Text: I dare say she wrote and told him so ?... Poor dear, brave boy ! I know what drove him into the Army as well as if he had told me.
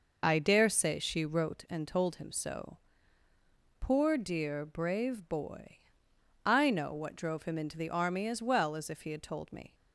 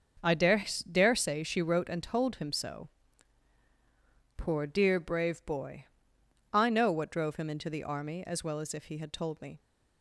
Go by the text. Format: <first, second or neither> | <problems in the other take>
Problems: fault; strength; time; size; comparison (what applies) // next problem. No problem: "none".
first | starts louder than the rest; until 1.4 s; 7 dB // says "dare" twice; at 0.9 s